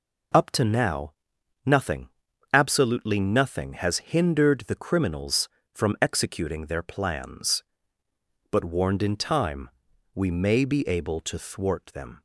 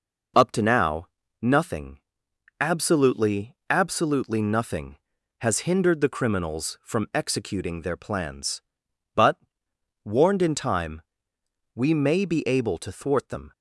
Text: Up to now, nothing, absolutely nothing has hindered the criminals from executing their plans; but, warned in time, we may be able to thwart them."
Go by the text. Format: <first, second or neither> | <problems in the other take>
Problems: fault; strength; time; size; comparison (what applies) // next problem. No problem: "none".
first | says "absolutely" twice; at 3.6 s